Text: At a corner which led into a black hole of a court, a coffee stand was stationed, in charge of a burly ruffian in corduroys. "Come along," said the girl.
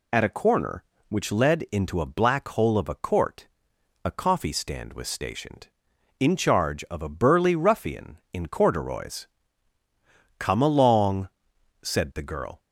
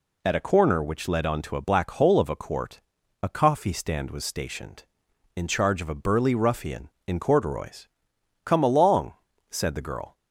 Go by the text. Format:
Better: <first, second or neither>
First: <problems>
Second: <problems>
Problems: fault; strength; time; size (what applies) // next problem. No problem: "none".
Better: first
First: none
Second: says "onto" for "into"; at 1.2 s